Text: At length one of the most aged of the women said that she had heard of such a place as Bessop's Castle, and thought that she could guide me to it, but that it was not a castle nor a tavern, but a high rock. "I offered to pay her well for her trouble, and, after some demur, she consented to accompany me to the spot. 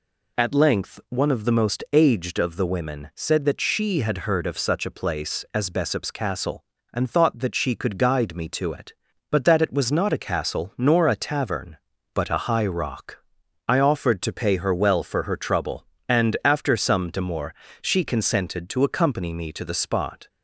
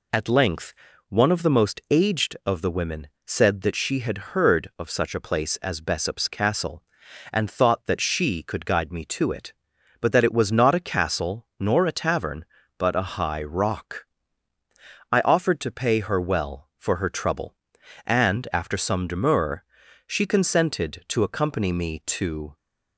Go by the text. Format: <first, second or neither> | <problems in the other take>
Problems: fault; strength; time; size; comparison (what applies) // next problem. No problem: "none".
first | pauses between "length" and "one"; slight; at 0.7 s; 0.36 s long // pauses between "women" and "said"; slight; at 3.0 s; 0.18 s long // stops before "the spot"; at 22.5 s